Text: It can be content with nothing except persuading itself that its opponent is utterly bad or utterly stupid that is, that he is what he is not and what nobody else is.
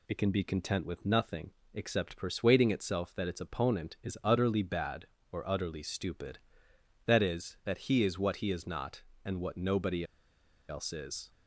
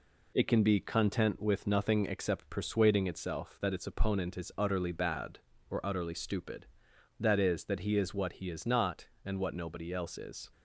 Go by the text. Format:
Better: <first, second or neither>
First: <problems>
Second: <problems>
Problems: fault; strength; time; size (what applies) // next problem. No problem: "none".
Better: second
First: pauses between "nothing" and "except"; slight; at 1.5 s; 0.22 s long // pauses between "nobody" and "else"; noticeable; at 10.0 s; 0.63 s long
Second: none